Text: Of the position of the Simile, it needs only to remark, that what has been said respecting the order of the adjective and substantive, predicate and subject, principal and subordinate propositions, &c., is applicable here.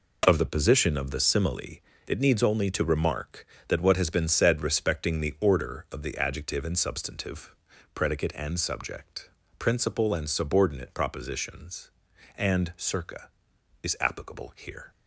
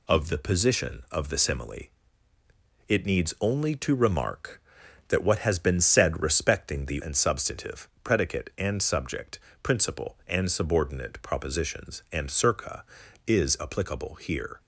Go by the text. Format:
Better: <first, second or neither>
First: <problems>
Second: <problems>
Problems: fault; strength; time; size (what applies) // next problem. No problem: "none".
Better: first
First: none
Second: skips "order of the adjective"; at 6.9 s